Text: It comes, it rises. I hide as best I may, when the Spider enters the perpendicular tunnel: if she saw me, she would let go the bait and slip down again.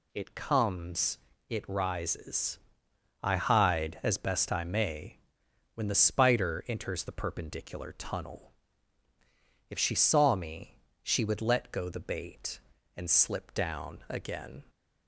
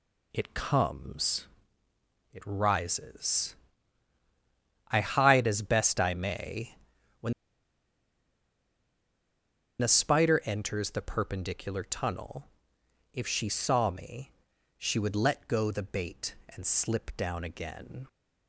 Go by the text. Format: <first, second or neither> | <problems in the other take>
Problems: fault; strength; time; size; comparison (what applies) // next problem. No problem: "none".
first | pauses between "when" and "the"; strong; at 7.3 s; 2.4 s long